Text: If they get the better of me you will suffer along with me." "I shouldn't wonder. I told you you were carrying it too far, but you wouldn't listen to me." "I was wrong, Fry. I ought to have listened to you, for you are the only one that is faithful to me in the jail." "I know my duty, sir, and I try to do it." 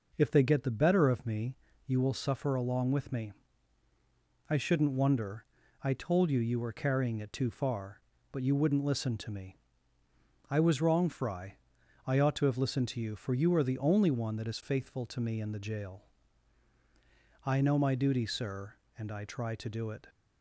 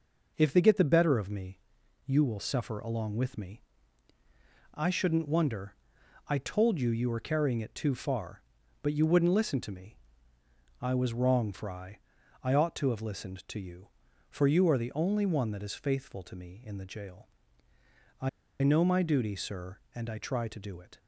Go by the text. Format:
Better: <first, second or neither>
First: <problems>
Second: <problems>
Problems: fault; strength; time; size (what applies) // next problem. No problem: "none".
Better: first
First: pauses between "me" and "you"; slight; at 1.5 s; 0.30 s long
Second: pauses between "me" and "you"; noticeable; at 1.5 s; 0.48 s long // pauses between "I" and "know"; slight; at 18.2 s; 0.32 s long